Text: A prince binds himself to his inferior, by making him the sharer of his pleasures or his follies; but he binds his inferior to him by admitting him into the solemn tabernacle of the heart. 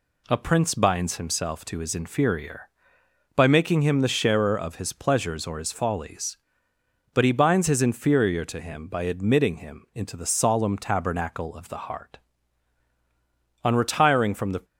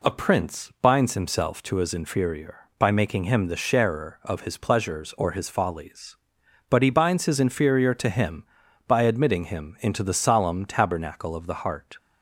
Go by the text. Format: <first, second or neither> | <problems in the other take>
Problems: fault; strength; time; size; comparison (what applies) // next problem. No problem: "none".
second | goes on to say "On retiring from the"; noticeable; from 13.6 s on; 1.0 s long